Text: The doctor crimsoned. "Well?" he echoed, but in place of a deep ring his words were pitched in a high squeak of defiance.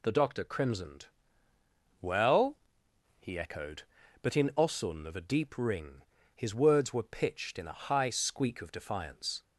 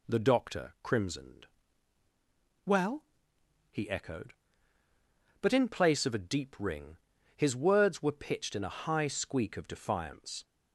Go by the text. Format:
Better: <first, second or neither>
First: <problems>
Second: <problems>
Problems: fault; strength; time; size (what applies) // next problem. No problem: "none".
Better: second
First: says "osun" for "place"; at 4.5 s // pauses between "ring" and "his"; slight; at 6.0 s; 0.34 s long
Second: pauses between "ring" and "his"; slight; at 6.9 s; 0.36 s long